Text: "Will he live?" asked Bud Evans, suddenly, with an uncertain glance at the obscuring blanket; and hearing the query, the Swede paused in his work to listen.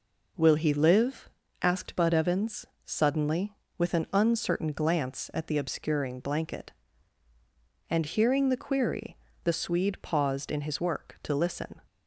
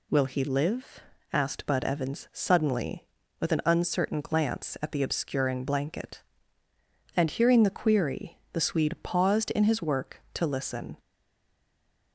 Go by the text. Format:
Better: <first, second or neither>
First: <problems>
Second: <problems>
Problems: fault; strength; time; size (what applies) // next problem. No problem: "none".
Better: first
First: none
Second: stays silent after the last word; noticeable; from 10.9 s on; 1.2 s long